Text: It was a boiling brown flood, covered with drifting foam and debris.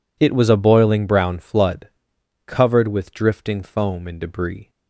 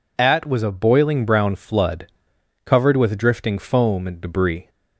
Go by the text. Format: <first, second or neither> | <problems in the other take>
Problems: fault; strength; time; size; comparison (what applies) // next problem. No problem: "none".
first | says "At" for "It"; at 0.1 s